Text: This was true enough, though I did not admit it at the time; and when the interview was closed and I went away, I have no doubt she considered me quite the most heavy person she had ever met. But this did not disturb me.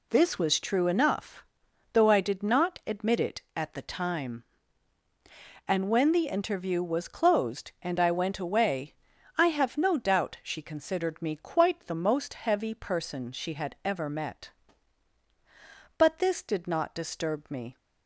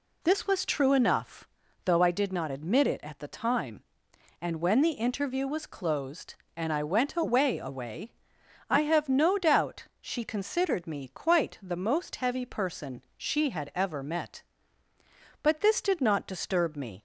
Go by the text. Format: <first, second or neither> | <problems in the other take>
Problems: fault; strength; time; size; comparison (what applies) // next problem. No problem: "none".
first | says "away" twice; at 7.5 s